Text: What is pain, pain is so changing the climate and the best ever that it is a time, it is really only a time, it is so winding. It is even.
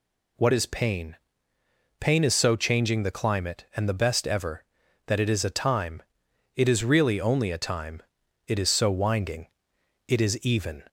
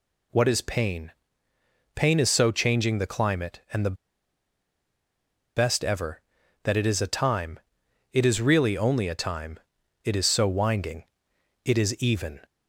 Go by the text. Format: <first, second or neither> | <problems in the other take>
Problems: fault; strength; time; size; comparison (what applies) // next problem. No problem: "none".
first | pauses between "the" and "best"; strong; at 3.9 s; 1.6 s long